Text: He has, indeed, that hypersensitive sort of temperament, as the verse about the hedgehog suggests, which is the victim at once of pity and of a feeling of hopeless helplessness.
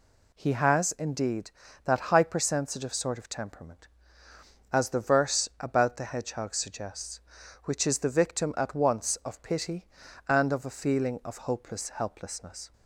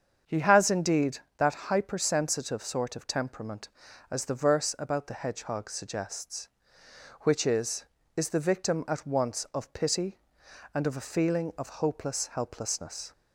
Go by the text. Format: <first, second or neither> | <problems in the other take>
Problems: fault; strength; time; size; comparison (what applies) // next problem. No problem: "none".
first | starts louder than the rest; until 1.4 s; 7 dB // says "is" twice; at 8.1 s